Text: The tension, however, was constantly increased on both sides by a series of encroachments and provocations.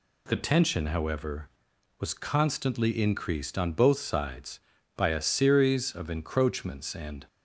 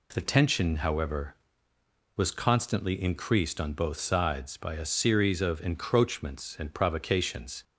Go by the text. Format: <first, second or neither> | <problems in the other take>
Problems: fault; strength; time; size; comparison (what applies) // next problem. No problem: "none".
second | stops before "provocations"; at 7.2 s